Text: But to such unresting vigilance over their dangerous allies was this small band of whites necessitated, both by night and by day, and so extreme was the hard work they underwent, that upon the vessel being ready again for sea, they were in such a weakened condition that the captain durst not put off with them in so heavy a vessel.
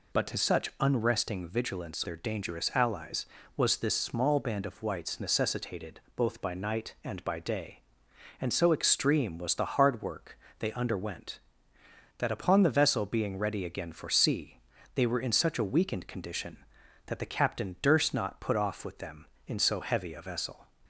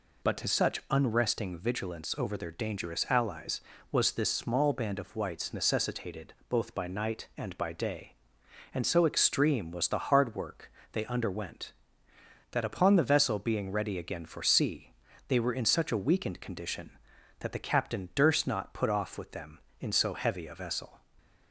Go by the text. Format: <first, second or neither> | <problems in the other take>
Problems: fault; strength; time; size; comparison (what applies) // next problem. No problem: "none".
second | skips "over"; at 2.0 s // pauses between "work" and "they"; slight; at 10.3 s; 0.22 s long; slight in the second